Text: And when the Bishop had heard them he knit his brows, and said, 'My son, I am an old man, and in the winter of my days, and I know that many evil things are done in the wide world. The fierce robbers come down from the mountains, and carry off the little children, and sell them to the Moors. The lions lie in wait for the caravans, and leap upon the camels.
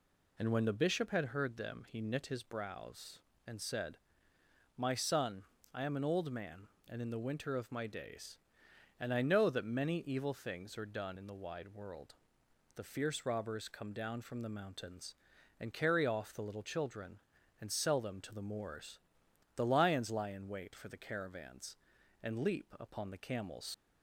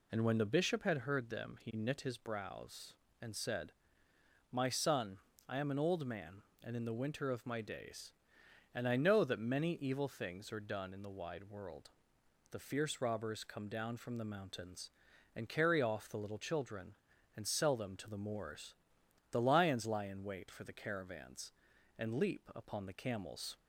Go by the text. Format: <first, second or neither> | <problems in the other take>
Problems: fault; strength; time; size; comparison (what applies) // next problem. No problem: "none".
second | leaves "camels" unfinished; at 23.7 s; 95 ms